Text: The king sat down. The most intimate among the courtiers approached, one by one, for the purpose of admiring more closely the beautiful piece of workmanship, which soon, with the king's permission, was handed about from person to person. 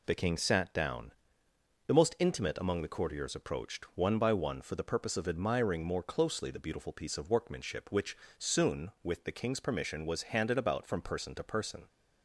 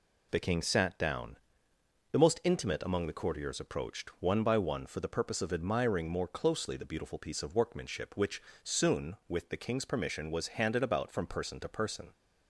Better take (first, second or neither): neither